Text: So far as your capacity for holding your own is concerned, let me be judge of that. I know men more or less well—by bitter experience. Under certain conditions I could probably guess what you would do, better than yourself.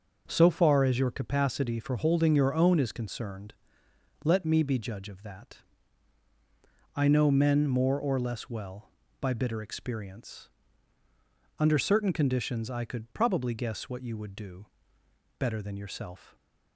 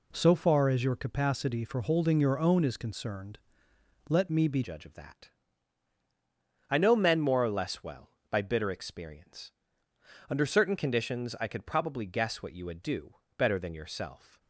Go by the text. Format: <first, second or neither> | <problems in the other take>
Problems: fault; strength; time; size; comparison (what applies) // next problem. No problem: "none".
first | changes voice at "judge"; from 4.6 s on; 9.7 s long